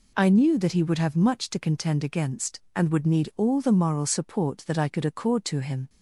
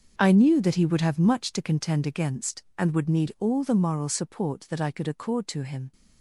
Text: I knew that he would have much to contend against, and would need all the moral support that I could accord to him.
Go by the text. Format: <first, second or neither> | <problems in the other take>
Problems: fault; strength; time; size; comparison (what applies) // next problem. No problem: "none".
first | gets quieter; strong; throughout; 14 dB